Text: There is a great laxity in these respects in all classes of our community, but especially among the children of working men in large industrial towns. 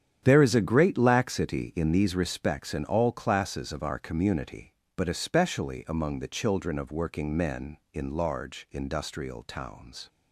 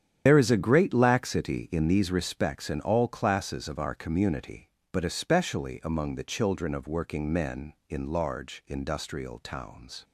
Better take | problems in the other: first | loses the start of "There"; at 0.2 s; 60 ms // starts louder than the rest; strong; until 1.2 s; 9 dB; strong in the first

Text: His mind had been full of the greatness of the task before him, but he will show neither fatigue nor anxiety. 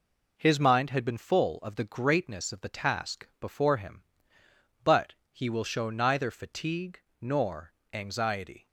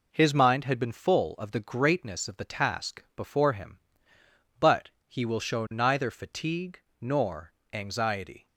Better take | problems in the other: neither | pauses between "but" and "he"; slight; the same in both // pauses between "fatigue" and "nor"; slight; the same in both // pauses between "nor" and "anxiety"; slight; the same in both

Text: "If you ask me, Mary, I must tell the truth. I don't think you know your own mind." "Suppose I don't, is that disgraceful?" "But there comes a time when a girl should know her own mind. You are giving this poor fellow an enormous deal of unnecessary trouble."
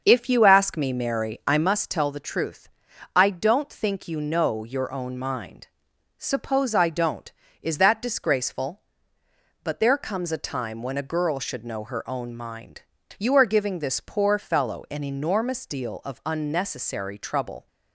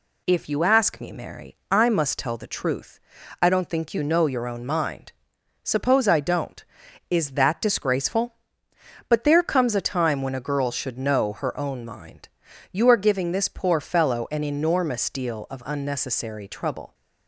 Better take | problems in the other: second | starts louder than the rest; until 1.7 s; 6.5 dB

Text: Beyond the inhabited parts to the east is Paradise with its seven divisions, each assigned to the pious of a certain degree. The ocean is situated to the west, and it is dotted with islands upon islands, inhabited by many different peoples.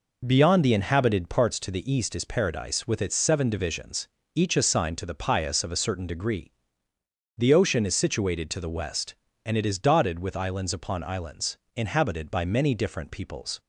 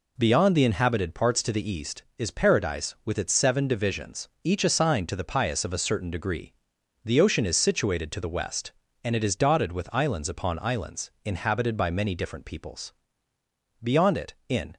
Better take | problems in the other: first | goes on to say "Beyond it in"; noticeable; from 13.8 s on; 0.94 s long

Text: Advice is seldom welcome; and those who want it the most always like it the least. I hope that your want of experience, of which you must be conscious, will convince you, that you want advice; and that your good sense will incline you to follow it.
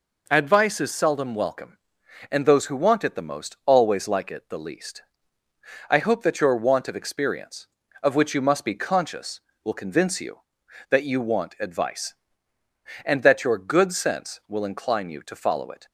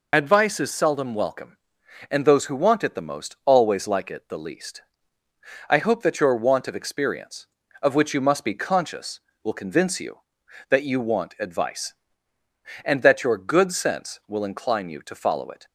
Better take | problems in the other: first | loses the start of "Advice"; at 0.1 s; 70 ms

